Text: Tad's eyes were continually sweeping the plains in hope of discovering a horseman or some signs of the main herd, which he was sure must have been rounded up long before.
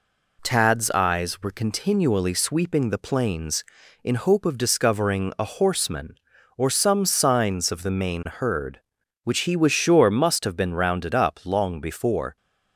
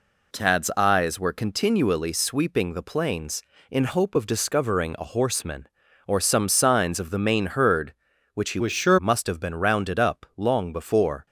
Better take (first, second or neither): first